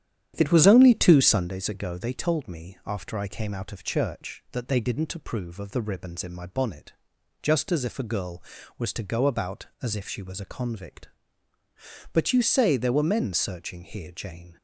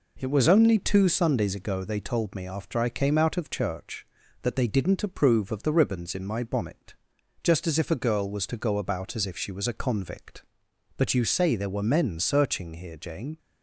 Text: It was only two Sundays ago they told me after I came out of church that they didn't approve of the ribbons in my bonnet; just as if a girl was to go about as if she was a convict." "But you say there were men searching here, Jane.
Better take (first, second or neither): second